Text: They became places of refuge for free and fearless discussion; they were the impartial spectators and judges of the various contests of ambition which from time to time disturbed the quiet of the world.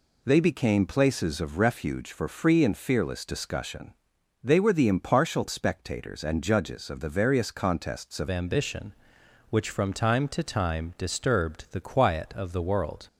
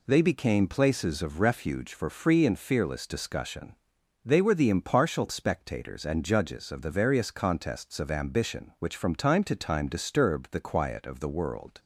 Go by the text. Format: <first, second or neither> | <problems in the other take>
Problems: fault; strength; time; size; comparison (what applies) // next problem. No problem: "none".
second | changes voice at "ambition"; from 8.2 s on; 4.8 s long